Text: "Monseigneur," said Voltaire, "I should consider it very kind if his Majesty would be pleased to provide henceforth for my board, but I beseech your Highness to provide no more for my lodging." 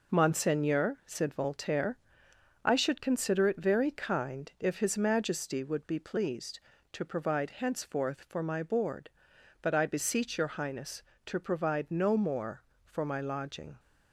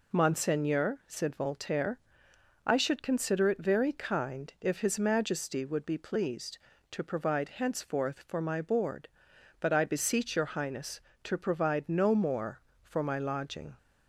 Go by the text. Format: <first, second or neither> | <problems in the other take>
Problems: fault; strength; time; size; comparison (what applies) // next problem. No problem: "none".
second | gets quieter; noticeable; throughout; 6 dB